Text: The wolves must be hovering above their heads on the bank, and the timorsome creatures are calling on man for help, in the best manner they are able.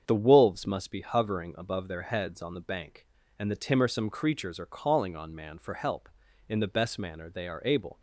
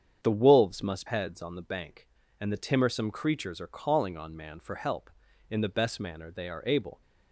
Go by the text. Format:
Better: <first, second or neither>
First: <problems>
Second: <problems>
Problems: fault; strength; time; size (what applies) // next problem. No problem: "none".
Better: first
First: starts louder than the rest; strong; until 1.0 s; 7.5 dB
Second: starts louder than the rest; strong; until 1.2 s; 7.5 dB // skips "be hovering above their"; at 1.0 s